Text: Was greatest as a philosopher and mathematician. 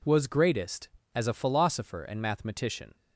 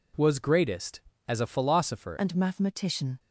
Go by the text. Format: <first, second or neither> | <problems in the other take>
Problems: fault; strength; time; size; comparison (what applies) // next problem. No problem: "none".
first | changes voice at "and"; from 2.1 s on; 1.0 s long